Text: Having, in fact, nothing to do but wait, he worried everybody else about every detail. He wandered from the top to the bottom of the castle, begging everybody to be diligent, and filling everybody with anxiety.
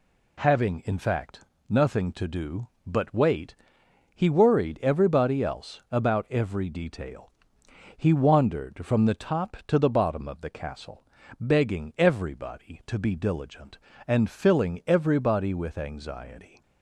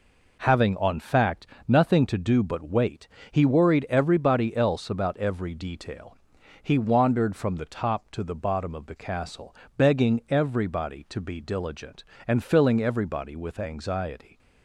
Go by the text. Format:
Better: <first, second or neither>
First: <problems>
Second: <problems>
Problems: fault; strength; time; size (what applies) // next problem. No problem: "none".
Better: first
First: none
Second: says "on" for "in"; at 0.7 s